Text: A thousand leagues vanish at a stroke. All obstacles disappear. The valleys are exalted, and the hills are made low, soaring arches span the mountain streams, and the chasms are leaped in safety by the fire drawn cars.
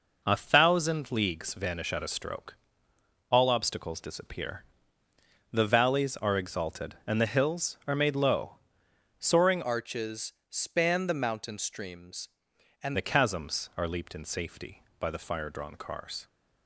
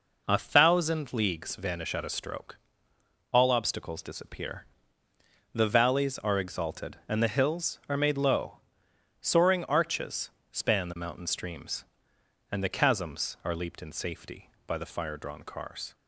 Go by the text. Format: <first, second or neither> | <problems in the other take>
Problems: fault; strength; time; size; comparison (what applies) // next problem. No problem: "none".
second | changes voice from "arches" to "and"; from 9.6 to 12.9 s; 3.3 s long // pauses between "arches" and "span"; slight; at 10.3 s; 0.18 s long; slight in the second